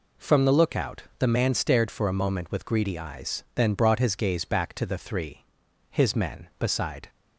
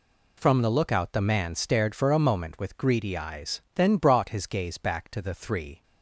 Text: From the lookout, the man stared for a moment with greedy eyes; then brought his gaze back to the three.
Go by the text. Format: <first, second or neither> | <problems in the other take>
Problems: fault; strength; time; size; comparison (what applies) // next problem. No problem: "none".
second | goes on to say "His men beside"; noticeable; from 5.9 s on; 1.1 s long